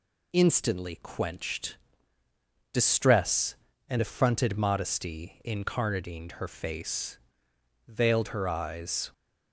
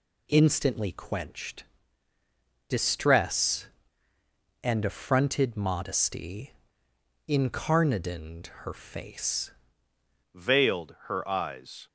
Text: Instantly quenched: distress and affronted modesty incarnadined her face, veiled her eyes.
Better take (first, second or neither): first